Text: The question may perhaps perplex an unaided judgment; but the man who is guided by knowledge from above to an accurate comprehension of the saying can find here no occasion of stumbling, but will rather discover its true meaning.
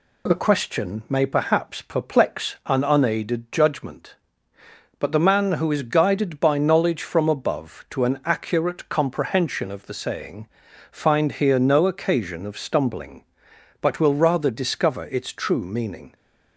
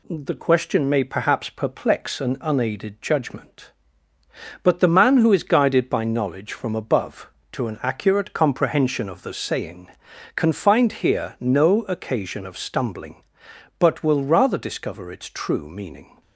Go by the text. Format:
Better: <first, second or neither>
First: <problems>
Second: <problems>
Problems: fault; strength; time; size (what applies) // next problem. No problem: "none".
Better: second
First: skips "can"; at 10.6 s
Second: none